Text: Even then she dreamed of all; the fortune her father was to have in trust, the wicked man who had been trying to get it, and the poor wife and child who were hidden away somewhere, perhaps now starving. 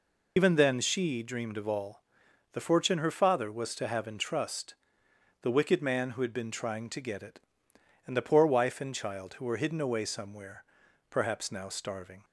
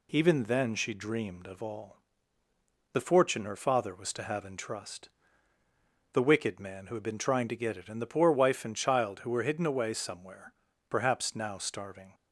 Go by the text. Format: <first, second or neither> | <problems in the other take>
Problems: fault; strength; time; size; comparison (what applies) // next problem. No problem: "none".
second | loses the start of "Even"; at 0.3 s; 60 ms